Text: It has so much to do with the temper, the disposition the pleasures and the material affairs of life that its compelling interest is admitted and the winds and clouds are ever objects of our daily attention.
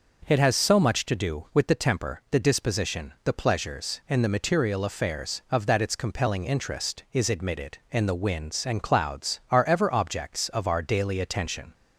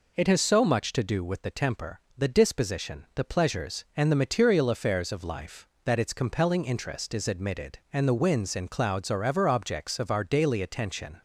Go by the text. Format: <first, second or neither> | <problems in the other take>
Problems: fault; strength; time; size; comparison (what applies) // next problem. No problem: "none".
second | skips "life"; at 5.6 s